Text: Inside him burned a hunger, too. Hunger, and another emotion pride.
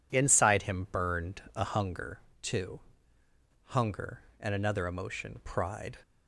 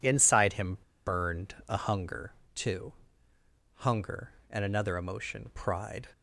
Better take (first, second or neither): first